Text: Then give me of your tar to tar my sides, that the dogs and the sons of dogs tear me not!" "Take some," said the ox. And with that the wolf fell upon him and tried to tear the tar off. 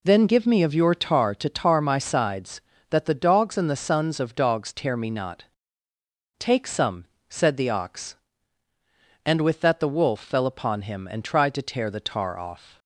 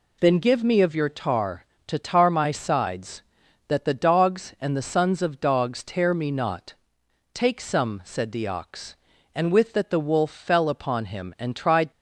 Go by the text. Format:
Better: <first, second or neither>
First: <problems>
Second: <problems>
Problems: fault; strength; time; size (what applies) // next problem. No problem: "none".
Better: first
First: none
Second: stops before "to tear the tar off"; at 11.9 s